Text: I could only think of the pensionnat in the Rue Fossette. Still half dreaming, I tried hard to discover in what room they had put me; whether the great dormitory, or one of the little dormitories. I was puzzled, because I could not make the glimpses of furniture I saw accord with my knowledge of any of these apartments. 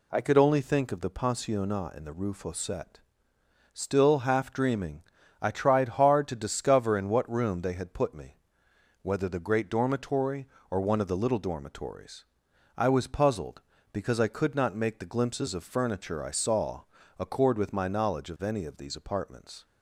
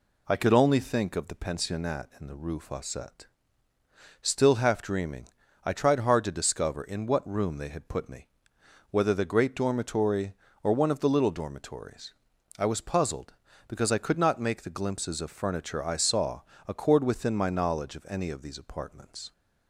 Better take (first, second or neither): first